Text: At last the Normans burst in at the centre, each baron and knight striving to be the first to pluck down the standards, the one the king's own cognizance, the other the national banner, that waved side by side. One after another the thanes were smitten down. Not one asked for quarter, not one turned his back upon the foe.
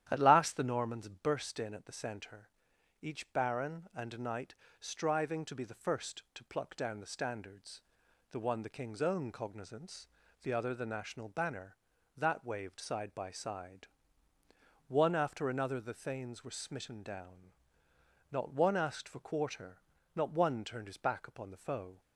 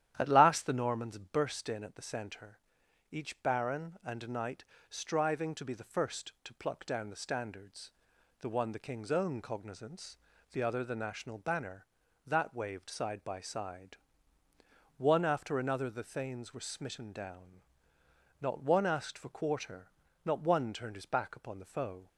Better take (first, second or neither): neither